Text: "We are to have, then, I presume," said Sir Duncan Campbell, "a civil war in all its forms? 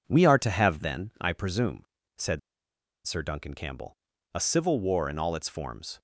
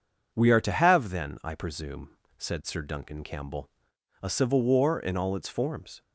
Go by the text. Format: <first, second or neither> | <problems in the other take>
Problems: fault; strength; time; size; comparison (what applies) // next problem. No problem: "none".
second | pauses between "said" and "Sir"; noticeable; at 2.3 s; 0.67 s long